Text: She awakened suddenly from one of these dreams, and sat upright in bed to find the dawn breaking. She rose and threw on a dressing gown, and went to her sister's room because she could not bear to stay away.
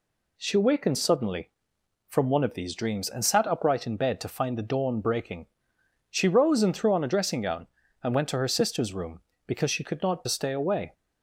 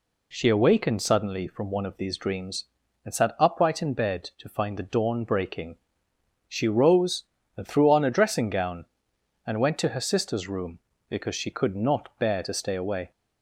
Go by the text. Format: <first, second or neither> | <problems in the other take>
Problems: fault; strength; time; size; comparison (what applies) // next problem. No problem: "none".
second | skips "bear to"; at 10.2 s